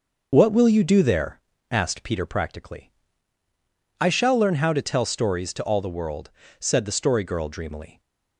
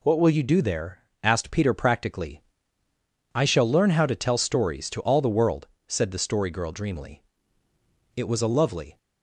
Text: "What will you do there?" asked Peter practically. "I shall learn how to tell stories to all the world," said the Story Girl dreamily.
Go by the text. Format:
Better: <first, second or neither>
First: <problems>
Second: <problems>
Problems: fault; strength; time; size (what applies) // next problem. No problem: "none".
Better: first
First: none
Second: goes on to say "It was a lovely"; noticeable; from 8.1 s on; 0.82 s long